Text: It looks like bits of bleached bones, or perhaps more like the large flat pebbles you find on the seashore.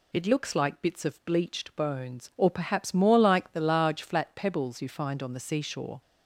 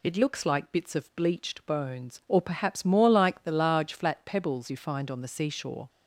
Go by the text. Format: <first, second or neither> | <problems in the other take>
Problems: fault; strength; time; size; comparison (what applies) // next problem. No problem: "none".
neither | none